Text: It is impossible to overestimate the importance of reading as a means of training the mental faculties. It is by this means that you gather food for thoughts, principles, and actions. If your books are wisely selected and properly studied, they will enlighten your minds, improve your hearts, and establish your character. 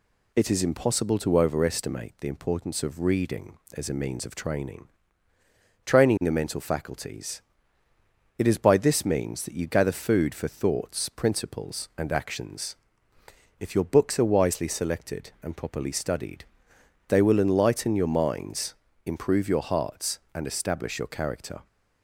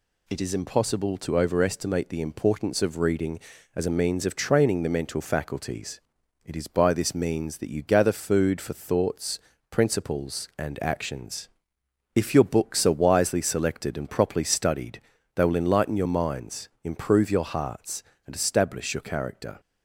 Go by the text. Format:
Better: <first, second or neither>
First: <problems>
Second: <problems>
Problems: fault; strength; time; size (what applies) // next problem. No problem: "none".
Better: second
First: says "training" twice; at 5.8 s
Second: none